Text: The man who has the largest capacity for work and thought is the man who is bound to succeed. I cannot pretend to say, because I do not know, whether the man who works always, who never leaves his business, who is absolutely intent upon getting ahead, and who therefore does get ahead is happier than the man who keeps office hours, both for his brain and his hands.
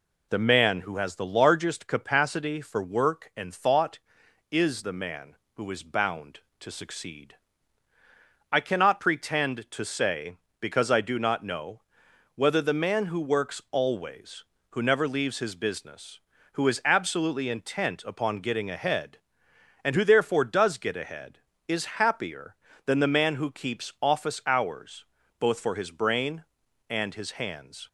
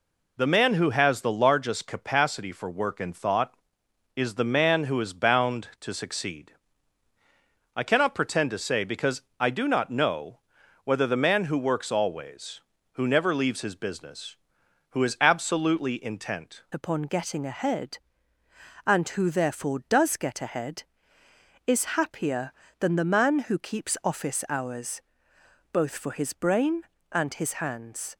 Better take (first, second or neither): first